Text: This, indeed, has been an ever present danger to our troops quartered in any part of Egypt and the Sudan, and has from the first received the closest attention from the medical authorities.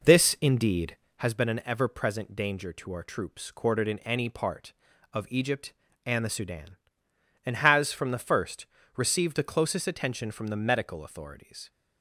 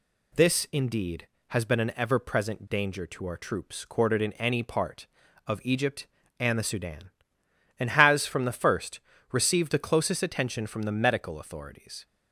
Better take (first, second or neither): second